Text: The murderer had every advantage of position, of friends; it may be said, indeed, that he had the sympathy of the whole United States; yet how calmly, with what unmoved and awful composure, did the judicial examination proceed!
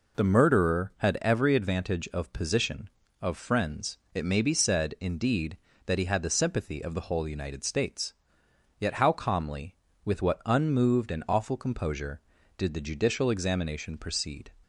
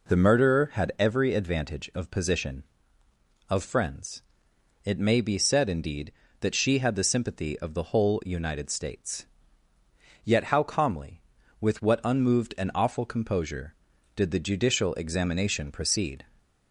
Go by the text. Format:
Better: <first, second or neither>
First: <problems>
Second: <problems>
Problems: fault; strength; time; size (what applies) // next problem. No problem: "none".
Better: first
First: none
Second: says "she" for "he"; at 6.5 s